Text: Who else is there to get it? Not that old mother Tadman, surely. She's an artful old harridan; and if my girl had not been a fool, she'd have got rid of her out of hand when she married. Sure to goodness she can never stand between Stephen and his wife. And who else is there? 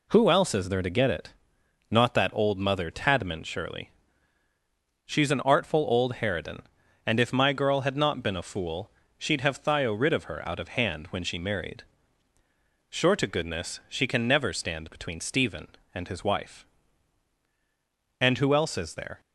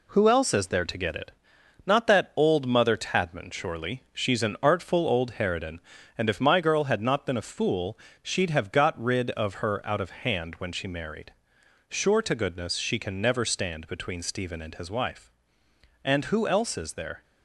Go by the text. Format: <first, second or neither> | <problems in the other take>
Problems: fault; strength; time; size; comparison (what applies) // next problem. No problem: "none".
second | says "thio" for "got"; at 9.6 s